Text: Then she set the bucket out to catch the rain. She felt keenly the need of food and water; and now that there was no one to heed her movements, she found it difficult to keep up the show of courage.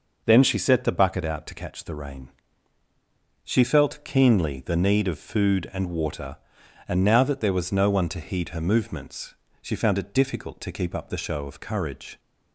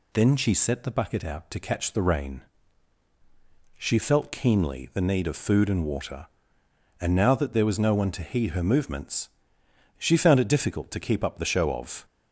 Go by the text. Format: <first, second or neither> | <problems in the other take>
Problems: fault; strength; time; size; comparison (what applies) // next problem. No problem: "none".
first | stops before "courage"; at 12.0 s